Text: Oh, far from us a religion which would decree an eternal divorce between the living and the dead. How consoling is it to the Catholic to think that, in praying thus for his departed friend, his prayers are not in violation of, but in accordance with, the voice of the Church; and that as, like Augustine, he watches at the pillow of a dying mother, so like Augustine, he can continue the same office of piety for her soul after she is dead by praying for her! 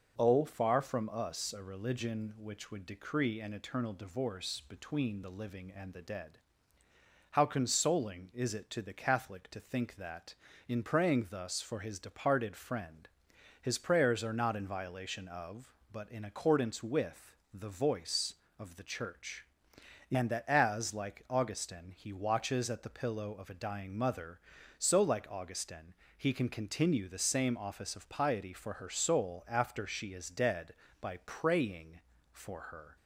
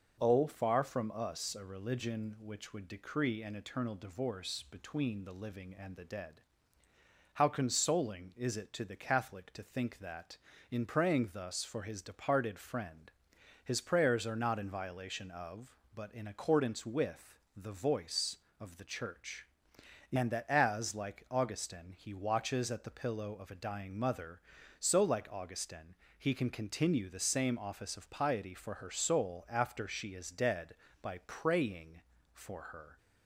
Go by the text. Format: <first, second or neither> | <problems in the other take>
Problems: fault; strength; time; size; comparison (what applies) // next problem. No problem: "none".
neither | none